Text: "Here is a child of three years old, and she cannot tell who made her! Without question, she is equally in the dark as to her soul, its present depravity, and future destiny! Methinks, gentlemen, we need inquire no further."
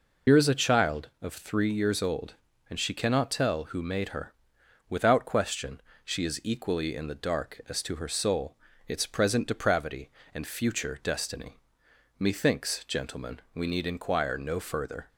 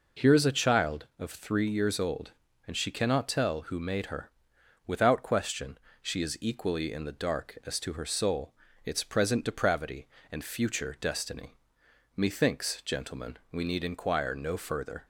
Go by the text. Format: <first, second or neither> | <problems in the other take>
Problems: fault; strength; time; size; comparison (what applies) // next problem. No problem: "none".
second | loses the start of "Here"; at 0.2 s; 80 ms